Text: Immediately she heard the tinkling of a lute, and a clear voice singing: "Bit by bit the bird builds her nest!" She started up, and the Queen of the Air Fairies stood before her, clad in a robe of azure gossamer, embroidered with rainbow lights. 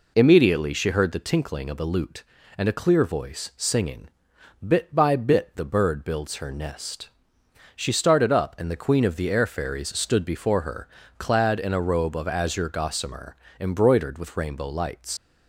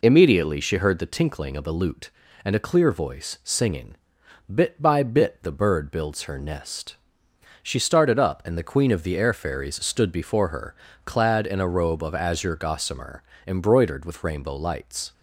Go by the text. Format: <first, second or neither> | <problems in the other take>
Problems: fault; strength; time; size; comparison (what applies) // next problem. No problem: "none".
second | leaves "lights" unfinished; at 15.1 s; 90 ms